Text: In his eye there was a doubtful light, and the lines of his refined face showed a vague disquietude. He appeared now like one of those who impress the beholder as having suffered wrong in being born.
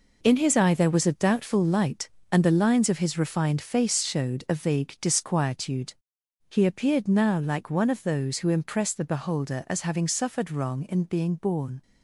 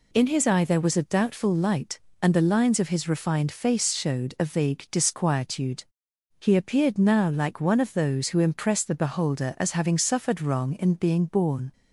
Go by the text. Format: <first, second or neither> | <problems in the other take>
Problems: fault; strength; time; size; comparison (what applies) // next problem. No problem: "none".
second | gets quieter; strong; throughout; 9 dB